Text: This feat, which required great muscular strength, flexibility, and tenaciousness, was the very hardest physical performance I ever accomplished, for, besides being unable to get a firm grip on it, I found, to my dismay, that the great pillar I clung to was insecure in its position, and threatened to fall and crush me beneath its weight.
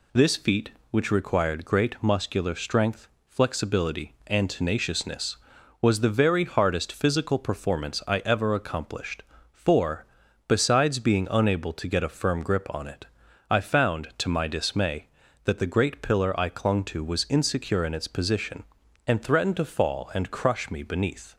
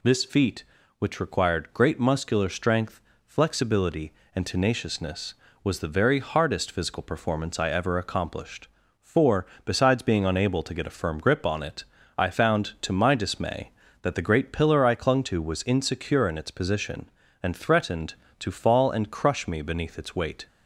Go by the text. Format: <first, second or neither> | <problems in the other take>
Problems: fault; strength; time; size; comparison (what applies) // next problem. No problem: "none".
second | stops before "its weight"; at 21.3 s